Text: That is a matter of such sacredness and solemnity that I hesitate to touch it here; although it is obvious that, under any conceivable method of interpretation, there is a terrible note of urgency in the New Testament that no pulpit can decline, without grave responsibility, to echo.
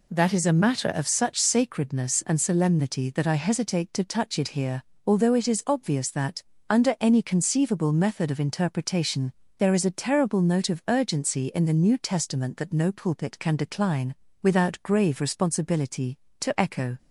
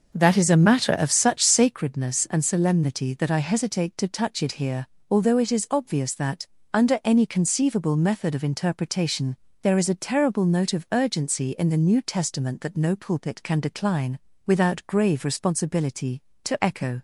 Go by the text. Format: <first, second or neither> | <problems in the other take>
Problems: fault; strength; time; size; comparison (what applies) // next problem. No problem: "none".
first | starts louder than the rest; noticeable; until 1.8 s; 6 dB